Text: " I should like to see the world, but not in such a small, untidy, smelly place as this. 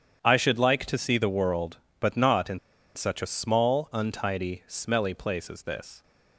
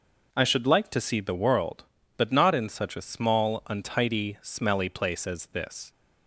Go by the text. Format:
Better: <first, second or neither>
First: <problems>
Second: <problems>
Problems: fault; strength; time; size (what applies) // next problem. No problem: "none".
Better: second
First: starts louder than the rest; strong; until 1.2 s; 8.5 dB // pauses between "in" and "such"; at 2.5 s; 0.37 s long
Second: none